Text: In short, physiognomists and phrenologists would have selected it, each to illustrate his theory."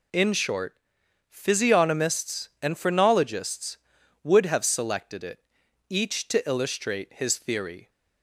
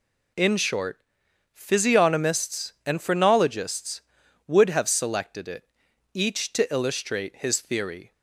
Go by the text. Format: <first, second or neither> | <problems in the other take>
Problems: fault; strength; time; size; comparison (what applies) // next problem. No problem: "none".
neither | none